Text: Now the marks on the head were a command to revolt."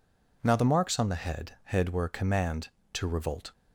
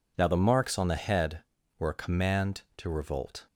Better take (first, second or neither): second